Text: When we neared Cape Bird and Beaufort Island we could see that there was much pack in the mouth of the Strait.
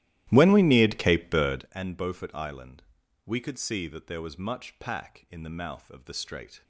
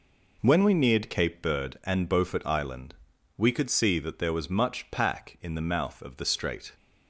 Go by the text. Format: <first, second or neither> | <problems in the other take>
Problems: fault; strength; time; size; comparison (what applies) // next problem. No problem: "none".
second | starts louder than the rest; strong; until 1.8 s; 14.5 dB // pauses between "Island" and "we"; at 2.8 s; 0.42 s long; also in the second